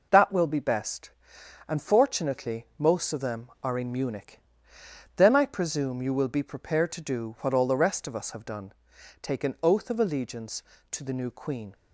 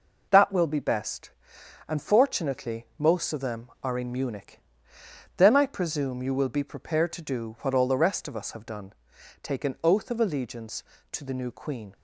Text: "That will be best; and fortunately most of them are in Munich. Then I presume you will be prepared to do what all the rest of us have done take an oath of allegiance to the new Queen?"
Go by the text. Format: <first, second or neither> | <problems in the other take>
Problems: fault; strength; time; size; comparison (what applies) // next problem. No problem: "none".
neither | pauses between "done" and "take"; noticeable; the same in both